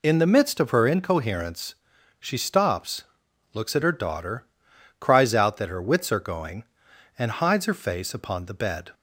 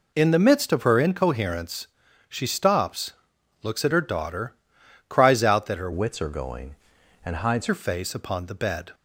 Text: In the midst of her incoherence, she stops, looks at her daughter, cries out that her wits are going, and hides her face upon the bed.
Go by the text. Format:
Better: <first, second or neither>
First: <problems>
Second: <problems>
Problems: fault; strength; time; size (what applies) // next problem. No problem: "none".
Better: first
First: none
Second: changes voice from "wits" to "hides"; from 5.9 to 7.6 s; 1.7 s long